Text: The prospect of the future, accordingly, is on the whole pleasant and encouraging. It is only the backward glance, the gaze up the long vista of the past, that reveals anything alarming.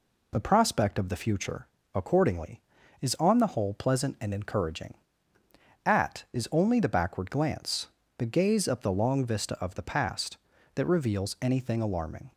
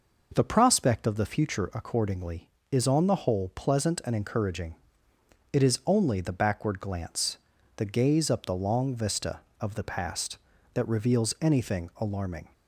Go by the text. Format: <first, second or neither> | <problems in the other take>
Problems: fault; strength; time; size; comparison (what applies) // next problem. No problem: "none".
second | says "At" for "It"; at 5.8 s